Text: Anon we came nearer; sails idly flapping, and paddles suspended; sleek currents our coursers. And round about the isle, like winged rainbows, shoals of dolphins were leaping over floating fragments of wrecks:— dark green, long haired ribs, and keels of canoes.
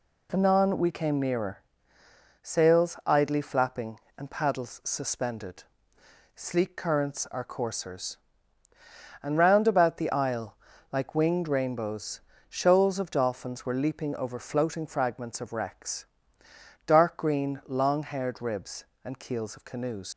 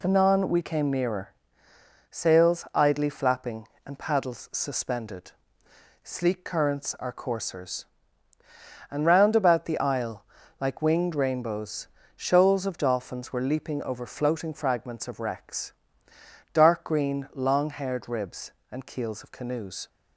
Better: second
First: leaves "canoes" unfinished; at 20.1 s; 90 ms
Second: none

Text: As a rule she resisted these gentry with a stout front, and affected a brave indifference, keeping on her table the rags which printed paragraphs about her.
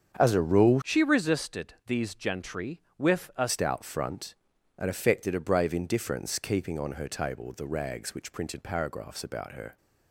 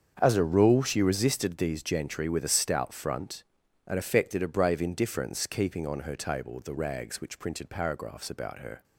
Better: second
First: starts louder than the rest; strong; until 1.2 s; 7.5 dB // changes voice from "she" to "a"; from 0.8 to 3.4 s; 2.6 s long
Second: starts louder than the rest; strong; until 1.2 s; 7 dB

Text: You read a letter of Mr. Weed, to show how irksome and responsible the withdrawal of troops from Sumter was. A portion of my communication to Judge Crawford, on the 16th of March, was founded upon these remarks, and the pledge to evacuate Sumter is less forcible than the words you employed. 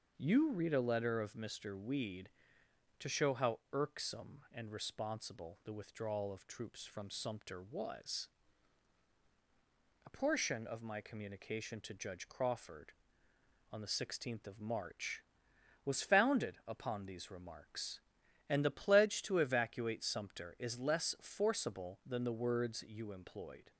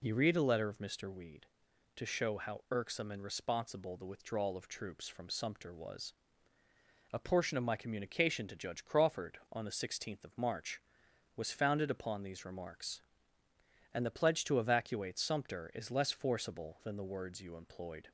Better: neither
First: none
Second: none

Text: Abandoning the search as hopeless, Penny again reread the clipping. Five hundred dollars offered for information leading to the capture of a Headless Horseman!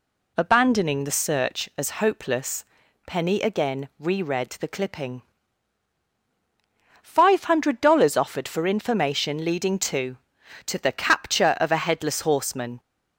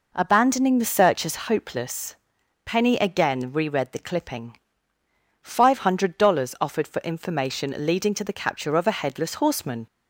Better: second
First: says "to" twice; at 10.6 s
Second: none

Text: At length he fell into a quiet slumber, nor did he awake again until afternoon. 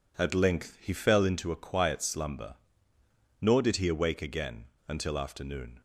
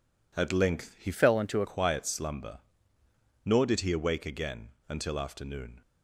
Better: first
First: pauses between "again" and "until"; slight; at 4.6 s; 0.23 s long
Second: changes voice from "fell" to "a"; from 1.1 to 1.6 s; 0.5 s long // pauses between "again" and "until"; slight; at 4.6 s; 0.20 s long

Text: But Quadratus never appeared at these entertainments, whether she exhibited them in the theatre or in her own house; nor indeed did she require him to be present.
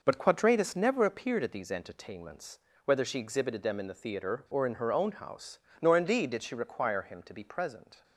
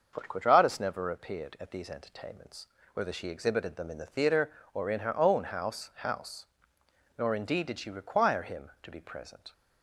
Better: first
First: none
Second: starts louder than the rest; until 1.1 s; 6 dB // says "house" twice; at 5.9 s

